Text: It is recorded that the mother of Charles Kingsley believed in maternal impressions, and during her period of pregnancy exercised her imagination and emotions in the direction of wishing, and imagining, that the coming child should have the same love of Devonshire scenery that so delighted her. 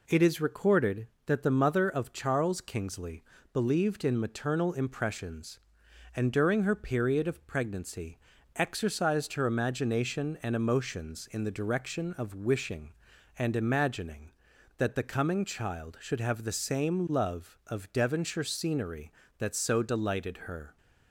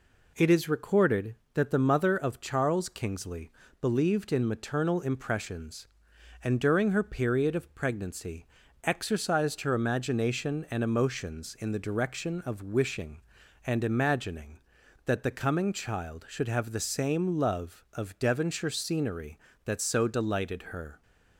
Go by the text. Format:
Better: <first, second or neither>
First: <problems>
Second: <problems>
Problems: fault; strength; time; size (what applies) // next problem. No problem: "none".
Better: neither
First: pauses between "Kingsley" and "believed"; slight; at 3.2 s; 0.30 s long // pauses between "pregnancy" and "exercised"; slight; at 8.1 s; 0.36 s long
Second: pauses between "Kingsley" and "believed"; slight; at 3.5 s; 0.30 s long // pauses between "pregnancy" and "exercised"; slight; at 8.4 s; 0.36 s long